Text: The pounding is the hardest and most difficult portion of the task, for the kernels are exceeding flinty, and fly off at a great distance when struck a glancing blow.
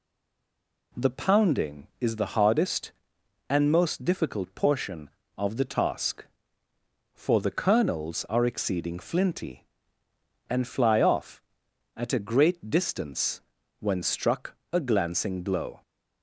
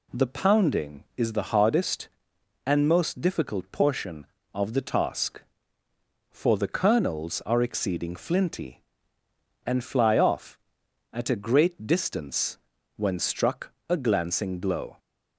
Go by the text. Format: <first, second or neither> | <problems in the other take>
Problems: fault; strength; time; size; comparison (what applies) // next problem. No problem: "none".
second | stays silent before the first word; slight; until 0.9 s; 0.9 s long // pauses between "distance" and "when"; at 13.3 s; 0.40 s long; also in the second // pauses between "struck" and "a"; slight; at 14.5 s; 0.16 s long; slight in the second